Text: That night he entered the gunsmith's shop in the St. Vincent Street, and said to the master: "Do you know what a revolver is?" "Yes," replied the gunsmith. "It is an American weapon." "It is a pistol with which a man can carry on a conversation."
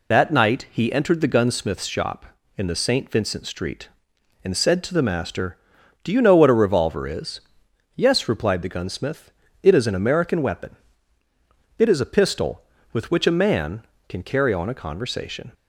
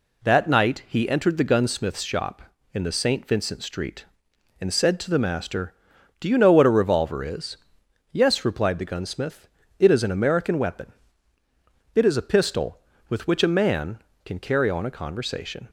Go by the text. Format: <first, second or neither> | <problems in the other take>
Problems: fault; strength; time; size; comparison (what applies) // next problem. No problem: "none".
second | loses the start of "That"; at 0.1 s; 35 ms